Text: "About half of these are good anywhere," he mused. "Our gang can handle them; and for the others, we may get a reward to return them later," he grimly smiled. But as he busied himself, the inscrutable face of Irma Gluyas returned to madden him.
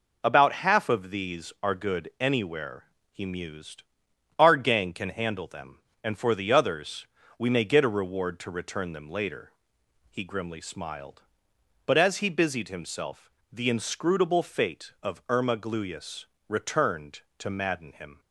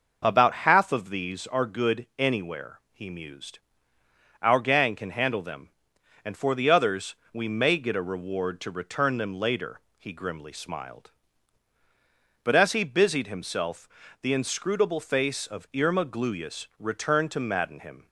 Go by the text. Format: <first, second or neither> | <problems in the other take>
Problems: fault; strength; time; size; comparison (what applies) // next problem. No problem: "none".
second | says "fate" for "face"; at 14.4 s // pauses between "Gluyas" and "returned"; slight; at 16.2 s; 0.24 s long